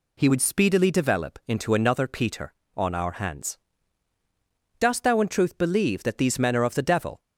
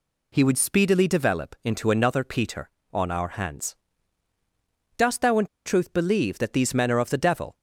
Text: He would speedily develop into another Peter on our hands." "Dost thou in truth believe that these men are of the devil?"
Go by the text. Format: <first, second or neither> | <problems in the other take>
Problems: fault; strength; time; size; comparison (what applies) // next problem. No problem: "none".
first | pauses between "in" and "truth"; slight; at 5.4 s; 0.20 s long